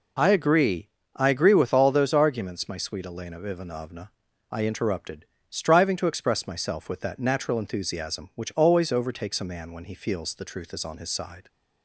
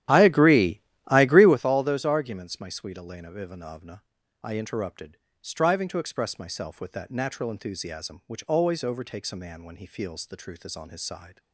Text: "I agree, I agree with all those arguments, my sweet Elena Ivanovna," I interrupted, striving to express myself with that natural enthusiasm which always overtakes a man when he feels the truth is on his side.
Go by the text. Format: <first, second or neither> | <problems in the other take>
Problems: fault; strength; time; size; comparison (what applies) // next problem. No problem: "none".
first | starts louder than the rest; strong; until 1.6 s; 11.5 dB